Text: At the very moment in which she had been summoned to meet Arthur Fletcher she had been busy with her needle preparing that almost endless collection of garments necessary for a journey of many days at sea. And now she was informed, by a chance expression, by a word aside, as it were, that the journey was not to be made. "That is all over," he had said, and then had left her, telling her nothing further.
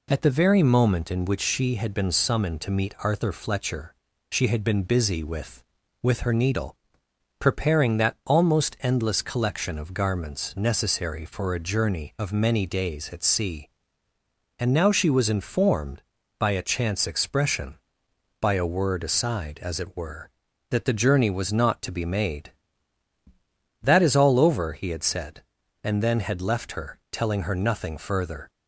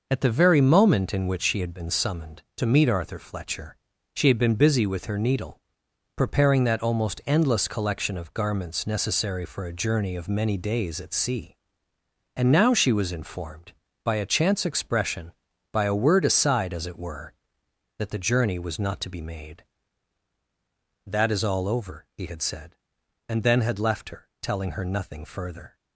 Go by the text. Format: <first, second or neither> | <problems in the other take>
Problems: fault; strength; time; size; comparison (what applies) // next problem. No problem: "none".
second | pauses between "Fletcher" and "she"; at 3.9 s; 0.38 s long; also in the second // says "with" twice; at 6.0 s // pauses between "needle" and "preparing"; noticeable; at 6.7 s; 0.62 s long; noticeable in the second